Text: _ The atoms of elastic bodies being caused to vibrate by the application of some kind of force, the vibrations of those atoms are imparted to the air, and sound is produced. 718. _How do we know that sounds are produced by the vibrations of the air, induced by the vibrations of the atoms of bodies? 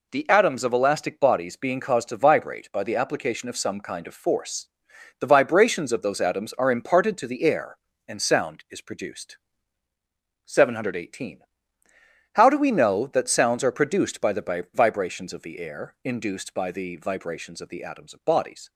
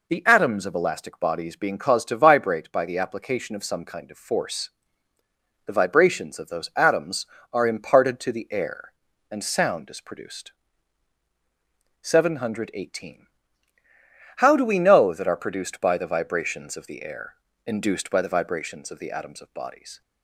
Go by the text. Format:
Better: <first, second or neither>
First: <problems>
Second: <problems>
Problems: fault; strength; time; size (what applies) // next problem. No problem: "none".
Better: first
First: none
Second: skips "sounds"; at 15.2 s